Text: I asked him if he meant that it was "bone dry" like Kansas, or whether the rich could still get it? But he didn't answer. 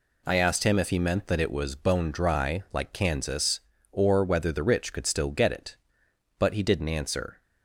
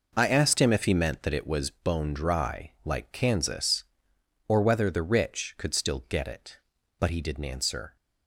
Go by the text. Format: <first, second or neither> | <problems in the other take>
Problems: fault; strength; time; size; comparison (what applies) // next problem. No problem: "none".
neither | none